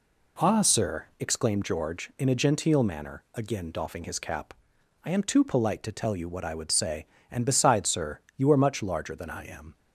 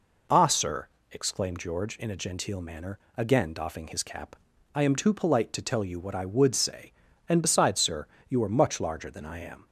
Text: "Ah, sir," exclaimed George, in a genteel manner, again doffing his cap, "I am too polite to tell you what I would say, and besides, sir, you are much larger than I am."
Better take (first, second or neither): neither